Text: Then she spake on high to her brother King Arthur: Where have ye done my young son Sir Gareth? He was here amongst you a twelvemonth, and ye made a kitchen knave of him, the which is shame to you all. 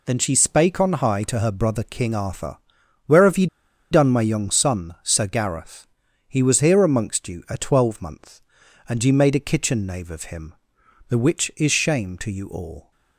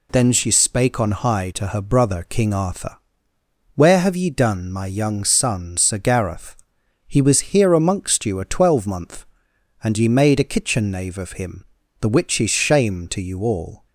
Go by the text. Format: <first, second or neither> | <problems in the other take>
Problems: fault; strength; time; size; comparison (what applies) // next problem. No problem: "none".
second | pauses between "ye" and "done"; at 3.4 s; 0.45 s long